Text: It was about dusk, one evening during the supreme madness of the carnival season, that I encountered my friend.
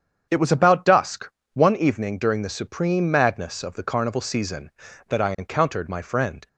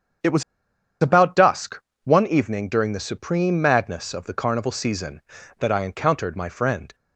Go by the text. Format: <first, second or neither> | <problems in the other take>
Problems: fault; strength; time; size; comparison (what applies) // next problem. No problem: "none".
first | starts louder than the rest; strong; until 2.0 s; 7.5 dB; strong in the first // pauses between "was" and "about"; noticeable; at 0.4 s; 0.59 s long